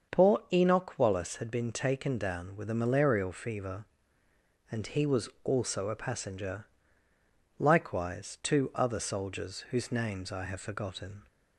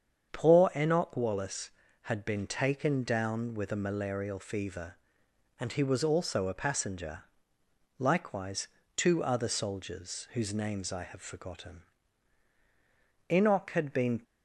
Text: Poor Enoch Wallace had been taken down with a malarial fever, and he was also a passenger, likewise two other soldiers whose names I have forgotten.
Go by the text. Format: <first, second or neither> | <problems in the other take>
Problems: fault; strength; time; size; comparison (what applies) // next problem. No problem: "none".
first | starts louder than the rest; strong; until 1.3 s; 7.5 dB; also in the first // pauses between "likewise" and "two"; slight; at 8.6 s; 0.28 s long // goes on to say "Enoch had been"; noticeable; from 13.2 s on; 0.92 s long